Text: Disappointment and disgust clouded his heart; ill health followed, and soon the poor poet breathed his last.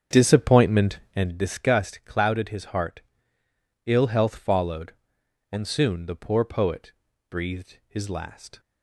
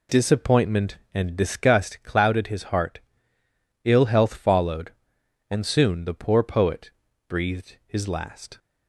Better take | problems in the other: second | starts louder than the rest; strong; until 1.3 s; 8 dB // pauses between "poet" and "breathed"; at 6.9 s; 0.38 s long; also in the second

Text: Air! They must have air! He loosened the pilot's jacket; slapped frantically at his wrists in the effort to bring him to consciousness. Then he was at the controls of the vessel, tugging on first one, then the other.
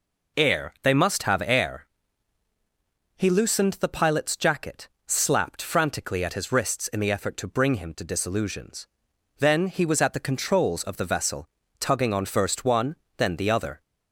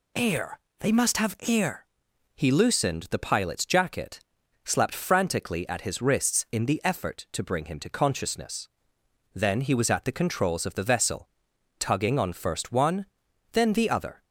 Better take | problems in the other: second | says "disillusions" for "consciousness"; at 8.0 s

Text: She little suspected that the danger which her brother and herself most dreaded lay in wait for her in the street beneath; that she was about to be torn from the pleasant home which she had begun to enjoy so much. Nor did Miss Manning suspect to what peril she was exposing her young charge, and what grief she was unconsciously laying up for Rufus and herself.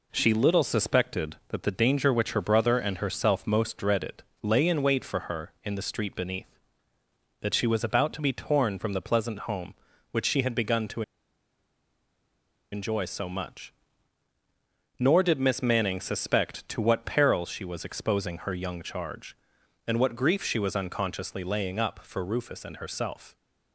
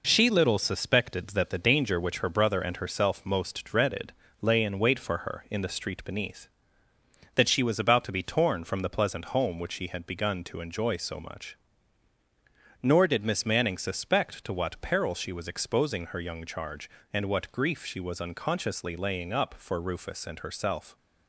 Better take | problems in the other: second | pauses between "dreaded" and "lay"; slight; at 4.2 s; 0.20 s long; slight in the second // pauses between "to" and "enjoy"; strong; at 11.0 s; 1.7 s long

